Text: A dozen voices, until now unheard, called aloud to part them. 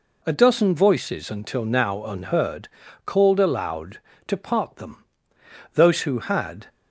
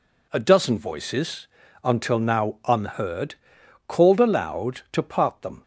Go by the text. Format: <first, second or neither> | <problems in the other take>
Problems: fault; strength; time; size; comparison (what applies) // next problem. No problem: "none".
second | goes on to say "Those who had"; noticeable; from 5.7 s on; 0.94 s long